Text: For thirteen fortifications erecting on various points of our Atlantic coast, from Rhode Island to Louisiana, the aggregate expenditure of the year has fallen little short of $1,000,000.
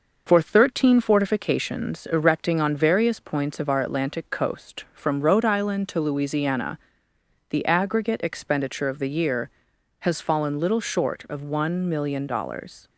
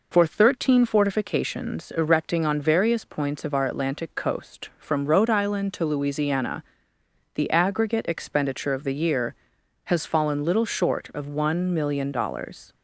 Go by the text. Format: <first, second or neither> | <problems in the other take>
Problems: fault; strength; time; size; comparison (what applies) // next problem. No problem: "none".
second | gets quieter; slight; throughout; 2.5 dB